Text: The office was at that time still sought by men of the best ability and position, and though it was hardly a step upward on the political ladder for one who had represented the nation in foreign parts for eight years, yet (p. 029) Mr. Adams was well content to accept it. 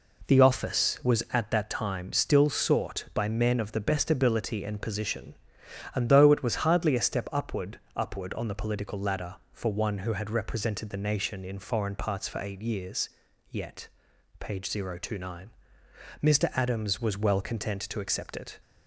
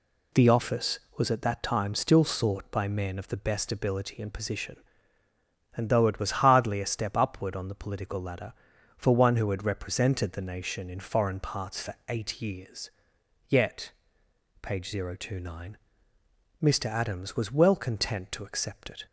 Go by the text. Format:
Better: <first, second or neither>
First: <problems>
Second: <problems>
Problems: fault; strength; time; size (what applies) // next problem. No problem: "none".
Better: second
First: says "upward" twice; at 7.9 s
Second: none